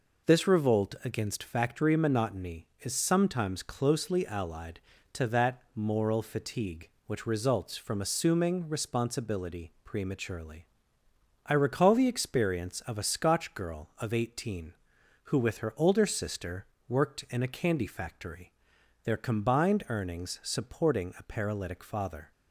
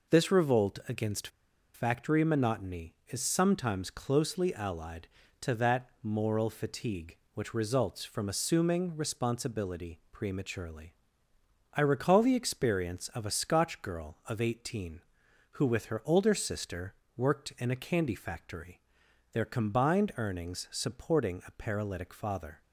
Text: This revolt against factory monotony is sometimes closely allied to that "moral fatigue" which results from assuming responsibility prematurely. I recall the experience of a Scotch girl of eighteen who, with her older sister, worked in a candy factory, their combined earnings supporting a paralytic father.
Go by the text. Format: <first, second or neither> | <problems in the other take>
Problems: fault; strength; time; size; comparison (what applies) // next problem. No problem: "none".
first | pauses between "against" and "factory"; noticeable; at 1.2 s; 0.46 s long